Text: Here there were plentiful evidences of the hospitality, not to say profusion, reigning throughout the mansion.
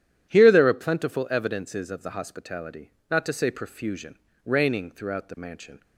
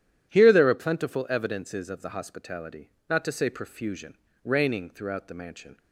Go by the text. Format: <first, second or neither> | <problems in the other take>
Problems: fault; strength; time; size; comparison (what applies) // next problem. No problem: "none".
neither | starts louder than the rest; strong; the same in both